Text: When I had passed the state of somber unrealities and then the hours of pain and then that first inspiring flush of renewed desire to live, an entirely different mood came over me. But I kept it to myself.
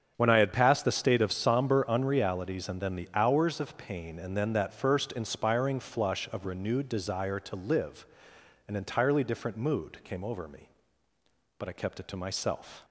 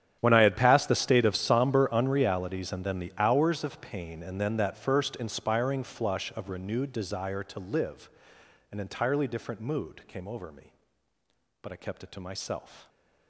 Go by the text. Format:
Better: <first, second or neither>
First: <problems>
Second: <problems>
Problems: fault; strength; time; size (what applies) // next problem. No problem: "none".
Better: first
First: starts louder than the rest; strong; until 1.1 s; 8 dB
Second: gets quieter; strong; throughout; 19 dB // starts louder than the rest; strong; until 1.2 s; 10 dB